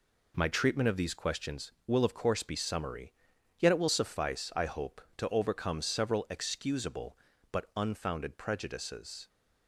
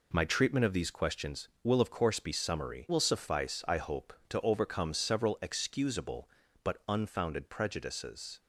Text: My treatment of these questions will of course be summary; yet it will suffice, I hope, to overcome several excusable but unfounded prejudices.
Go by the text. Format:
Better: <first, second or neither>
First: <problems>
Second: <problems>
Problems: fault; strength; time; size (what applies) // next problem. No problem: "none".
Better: first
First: none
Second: skips "yet it"; at 2.8 s